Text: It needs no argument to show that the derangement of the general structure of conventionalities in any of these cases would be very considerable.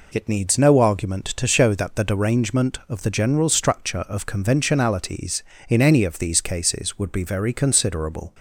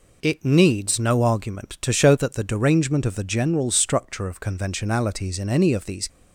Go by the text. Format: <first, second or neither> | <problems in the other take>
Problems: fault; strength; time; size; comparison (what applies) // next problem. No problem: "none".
first | stops before "cases would be very considerable"; at 6.0 s